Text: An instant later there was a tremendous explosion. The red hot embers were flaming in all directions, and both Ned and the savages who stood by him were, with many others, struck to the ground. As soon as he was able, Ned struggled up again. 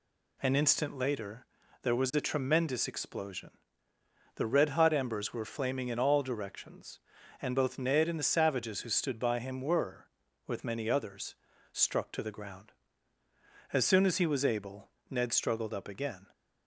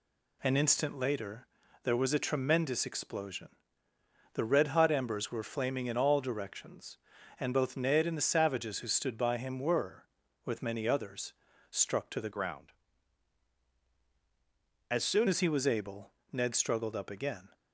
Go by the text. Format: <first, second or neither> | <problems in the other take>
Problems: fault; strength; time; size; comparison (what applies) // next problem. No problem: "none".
first | pauses between "later" and "there"; slight; at 1.4 s; 0.36 s long; slight in the first // changes voice from "ground" to "soon"; from 12.3 to 15.2 s; 2.9 s long